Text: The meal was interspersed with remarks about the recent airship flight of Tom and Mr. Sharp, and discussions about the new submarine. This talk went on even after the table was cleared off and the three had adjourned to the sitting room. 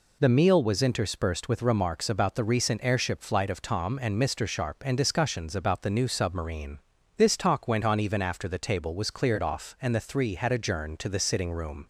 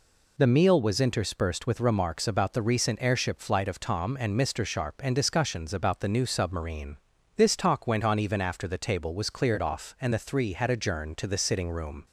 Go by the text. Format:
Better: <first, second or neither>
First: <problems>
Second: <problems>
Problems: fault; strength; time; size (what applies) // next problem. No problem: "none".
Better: neither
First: none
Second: none